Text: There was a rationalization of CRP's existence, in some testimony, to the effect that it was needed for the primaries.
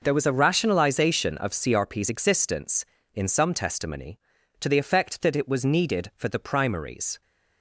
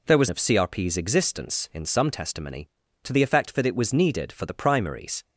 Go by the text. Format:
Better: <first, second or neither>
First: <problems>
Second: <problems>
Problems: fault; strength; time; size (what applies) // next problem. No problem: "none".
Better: first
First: none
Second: skips "a rationalization"; at 0.2 s